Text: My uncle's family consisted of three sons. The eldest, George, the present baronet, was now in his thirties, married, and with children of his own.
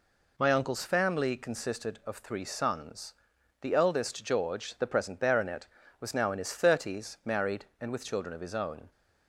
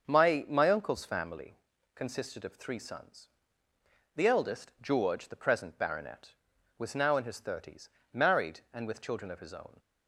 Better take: first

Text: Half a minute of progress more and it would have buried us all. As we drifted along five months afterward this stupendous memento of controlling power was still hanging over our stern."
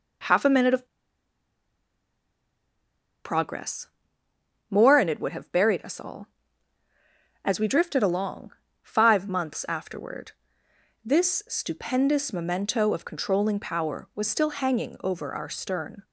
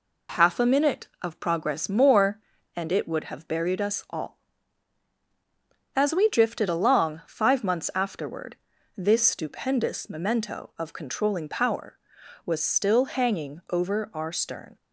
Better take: second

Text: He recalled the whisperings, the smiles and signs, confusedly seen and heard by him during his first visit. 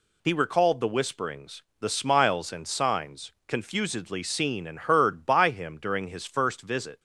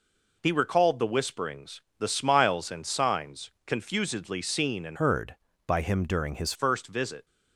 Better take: first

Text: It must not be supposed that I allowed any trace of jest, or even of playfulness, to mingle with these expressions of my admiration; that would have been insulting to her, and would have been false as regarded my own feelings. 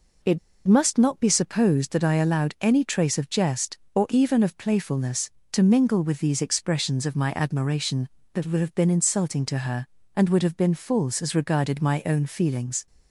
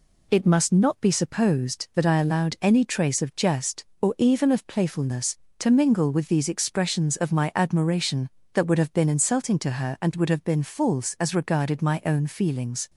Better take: second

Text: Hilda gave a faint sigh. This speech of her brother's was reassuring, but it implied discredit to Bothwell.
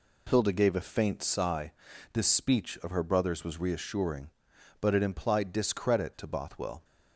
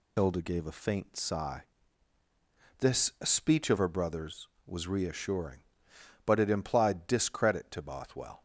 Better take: first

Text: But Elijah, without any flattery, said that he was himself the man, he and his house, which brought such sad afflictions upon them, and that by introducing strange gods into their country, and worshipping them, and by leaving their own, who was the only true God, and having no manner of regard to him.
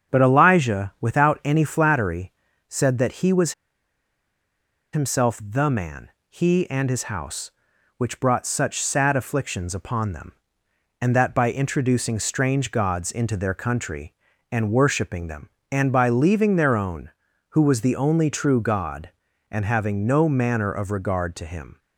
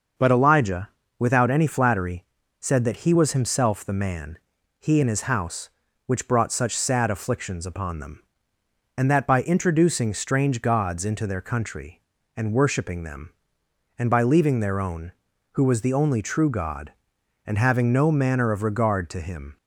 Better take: second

